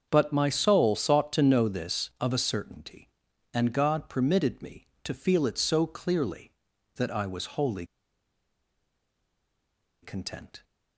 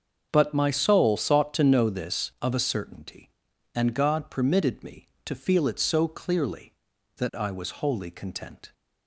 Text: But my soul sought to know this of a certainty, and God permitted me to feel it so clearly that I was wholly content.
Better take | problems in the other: second | starts louder than the rest; until 1.1 s; 6.5 dB; also in the second // pauses between "wholly" and "content"; strong; at 7.8 s; 2.1 s long

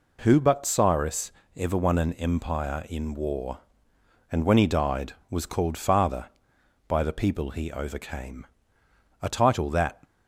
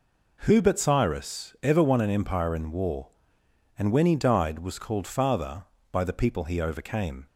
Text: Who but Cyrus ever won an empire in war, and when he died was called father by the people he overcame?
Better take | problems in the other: second | pauses between "Cyrus" and "ever"; slight; at 1.3 s; 0.24 s long // goes on to say "a title that"; noticeable; from 9.2 s on; 0.80 s long

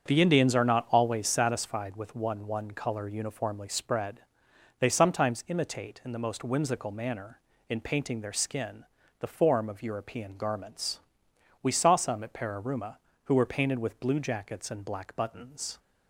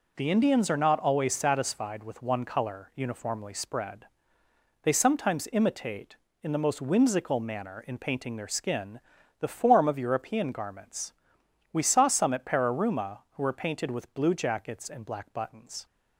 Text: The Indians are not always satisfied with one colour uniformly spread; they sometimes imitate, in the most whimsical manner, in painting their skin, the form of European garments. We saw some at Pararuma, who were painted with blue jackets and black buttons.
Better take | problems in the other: second | starts louder than the rest; strong; until 1.1 s; 7 dB // says "one" twice; at 2.4 s

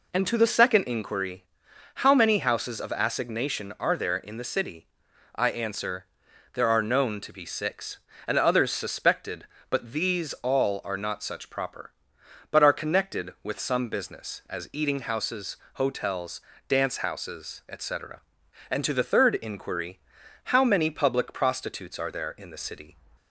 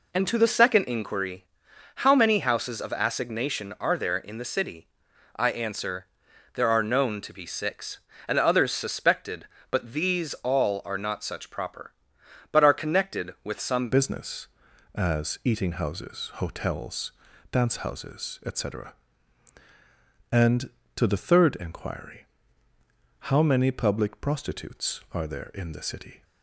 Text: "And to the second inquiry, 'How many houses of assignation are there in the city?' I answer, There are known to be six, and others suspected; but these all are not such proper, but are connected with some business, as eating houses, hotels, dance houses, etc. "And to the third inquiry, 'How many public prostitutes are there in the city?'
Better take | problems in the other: first | changes voice at "business"; from 13.9 s on; 12.3 s long

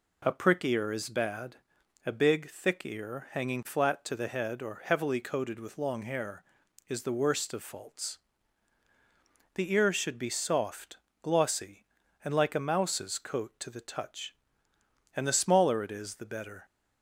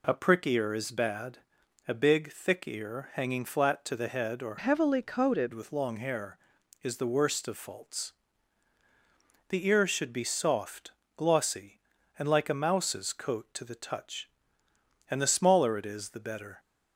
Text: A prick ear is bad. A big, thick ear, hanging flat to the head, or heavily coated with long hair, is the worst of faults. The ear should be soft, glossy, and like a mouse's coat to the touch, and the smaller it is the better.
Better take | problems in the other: first | changes voice from "heavily" to "coated"; from 4.5 to 5.5 s; 1.0 s long

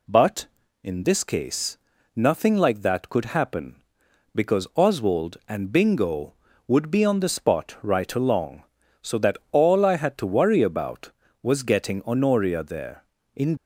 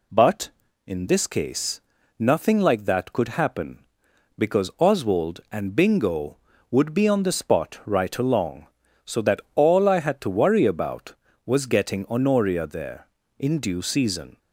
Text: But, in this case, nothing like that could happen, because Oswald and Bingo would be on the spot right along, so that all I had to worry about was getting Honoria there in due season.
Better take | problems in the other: second | stops before "due season"; at 13.5 s

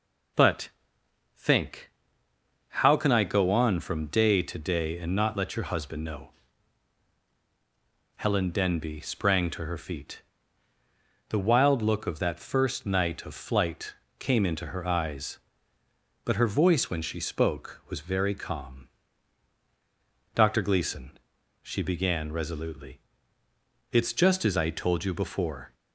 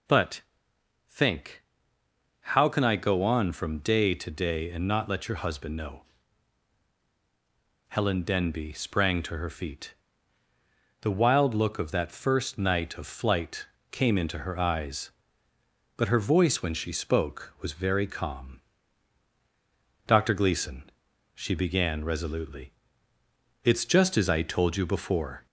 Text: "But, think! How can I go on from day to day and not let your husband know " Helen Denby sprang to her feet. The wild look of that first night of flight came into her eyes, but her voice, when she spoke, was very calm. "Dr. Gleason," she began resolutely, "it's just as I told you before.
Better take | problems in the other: first | gets louder; noticeable; throughout; 5.5 dB // pauses between "flight" and "came"; slight; at 13.6 s; 0.24 s long; slight in the first

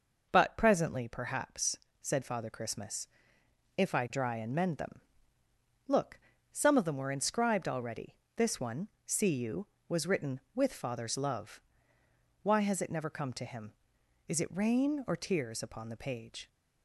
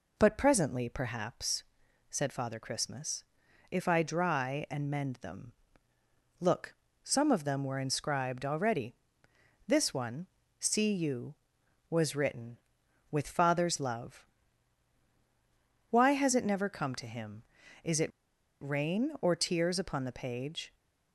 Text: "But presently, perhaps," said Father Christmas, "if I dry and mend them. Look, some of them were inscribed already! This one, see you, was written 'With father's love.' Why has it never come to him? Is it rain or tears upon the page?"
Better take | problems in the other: first | pauses between "it" and "rain"; noticeable; at 18.1 s; 0.51 s long

